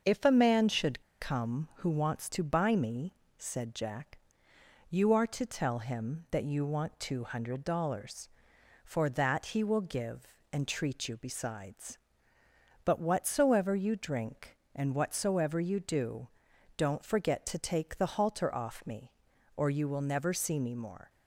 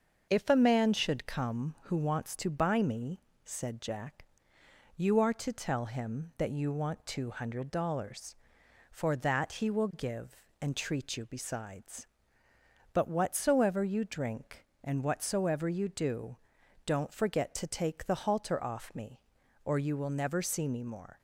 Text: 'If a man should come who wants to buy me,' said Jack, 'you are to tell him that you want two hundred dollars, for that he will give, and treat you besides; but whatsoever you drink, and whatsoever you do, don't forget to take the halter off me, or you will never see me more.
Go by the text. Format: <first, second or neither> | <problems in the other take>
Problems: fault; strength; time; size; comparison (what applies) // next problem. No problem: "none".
second | starts louder than the rest; until 1.2 s; 6.5 dB; also in the second // pauses between "should" and "come"; slight; at 1.0 s; 0.19 s long